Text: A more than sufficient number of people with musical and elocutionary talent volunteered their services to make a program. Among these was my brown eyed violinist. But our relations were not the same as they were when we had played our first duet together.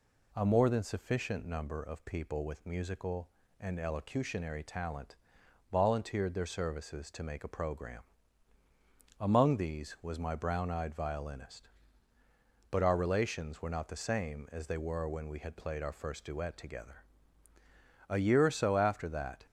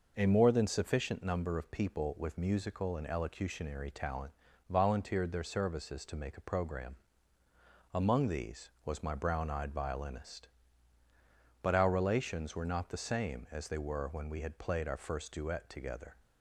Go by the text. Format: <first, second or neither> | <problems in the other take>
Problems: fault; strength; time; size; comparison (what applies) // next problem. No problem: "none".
second | pauses between "talent" and "volunteered"; noticeable; at 5.1 s; 0.54 s long; slight in the second // goes on to say "A year or so after that"; from 18.0 s on; 1.3 s long